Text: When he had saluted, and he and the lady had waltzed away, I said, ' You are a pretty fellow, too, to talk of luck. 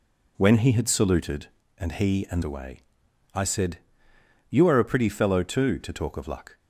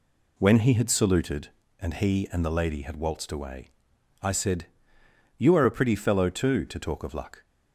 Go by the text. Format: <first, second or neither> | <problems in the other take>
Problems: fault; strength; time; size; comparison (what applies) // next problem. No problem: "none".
second | skips "the lady had waltzed"; at 2.4 s